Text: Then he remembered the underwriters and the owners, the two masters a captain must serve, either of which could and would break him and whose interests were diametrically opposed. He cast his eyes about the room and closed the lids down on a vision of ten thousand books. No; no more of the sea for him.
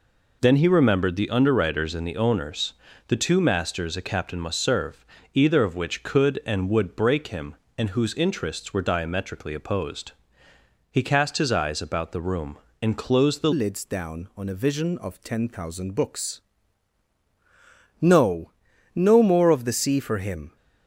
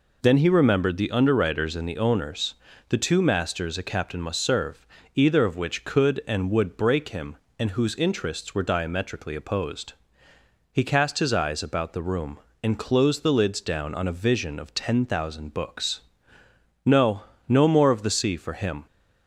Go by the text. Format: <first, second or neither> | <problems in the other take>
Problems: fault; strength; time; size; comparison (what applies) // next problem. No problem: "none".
second | changes voice at "lids"; from 13.5 s on; 7.0 s long